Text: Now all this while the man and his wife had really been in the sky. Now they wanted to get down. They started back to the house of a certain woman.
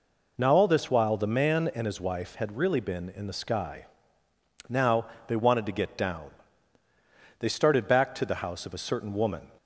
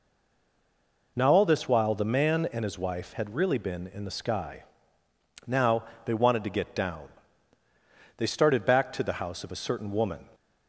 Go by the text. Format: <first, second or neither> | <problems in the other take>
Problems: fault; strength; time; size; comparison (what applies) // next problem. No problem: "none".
first | stays silent before the first word; until 1.1 s; 1.1 s long // pauses between "Now" and "they"; slight; at 5.8 s; 0.22 s long; slight in the first